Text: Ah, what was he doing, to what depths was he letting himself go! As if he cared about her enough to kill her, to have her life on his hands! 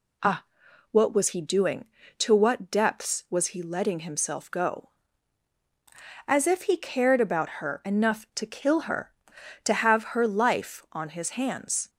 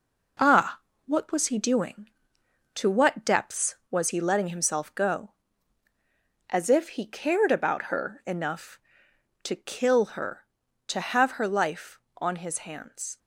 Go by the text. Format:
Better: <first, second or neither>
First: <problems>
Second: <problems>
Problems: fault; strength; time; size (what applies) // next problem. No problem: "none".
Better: first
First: none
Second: gets quieter; noticeable; throughout; 5.5 dB